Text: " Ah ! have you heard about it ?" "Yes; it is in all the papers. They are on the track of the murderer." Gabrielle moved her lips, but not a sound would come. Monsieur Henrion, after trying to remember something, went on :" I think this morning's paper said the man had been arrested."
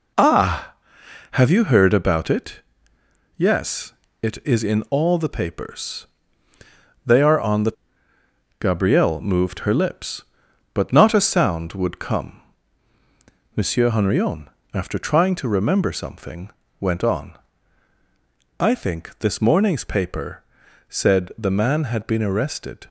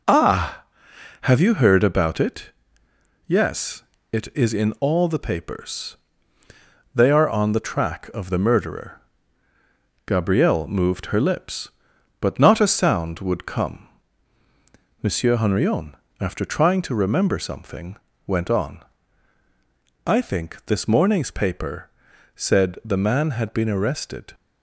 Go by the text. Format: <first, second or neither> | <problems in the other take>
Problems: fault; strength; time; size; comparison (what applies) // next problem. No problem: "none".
second | skips "track of the murderer"; at 8.1 s // pauses between "paper" and "said"; at 20.4 s; 0.44 s long; also in the second